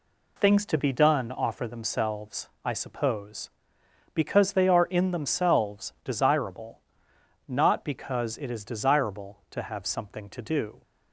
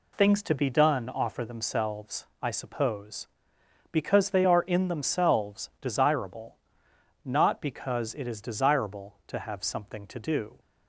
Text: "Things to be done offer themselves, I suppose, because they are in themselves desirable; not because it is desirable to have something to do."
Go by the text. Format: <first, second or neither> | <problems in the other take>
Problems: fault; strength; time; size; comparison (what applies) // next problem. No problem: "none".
neither | none